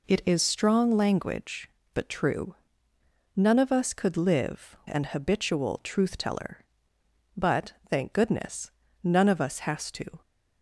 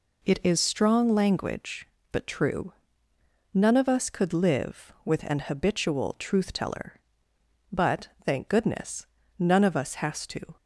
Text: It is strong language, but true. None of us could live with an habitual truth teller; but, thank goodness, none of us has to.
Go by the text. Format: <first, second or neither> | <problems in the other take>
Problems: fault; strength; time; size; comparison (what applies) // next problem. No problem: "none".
second | skips "with"; at 4.8 s